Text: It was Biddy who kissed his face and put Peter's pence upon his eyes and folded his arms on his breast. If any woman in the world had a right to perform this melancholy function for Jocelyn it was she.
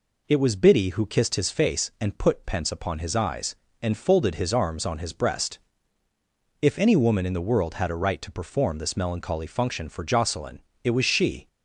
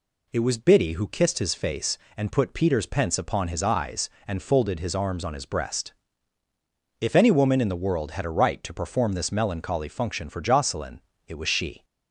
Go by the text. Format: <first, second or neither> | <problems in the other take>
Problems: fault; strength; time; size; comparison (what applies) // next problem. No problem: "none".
second | skips "Peter's"; at 2.4 s // pauses between "Jocelyn" and "it"; slight; at 10.5 s; 0.24 s long; slight in the second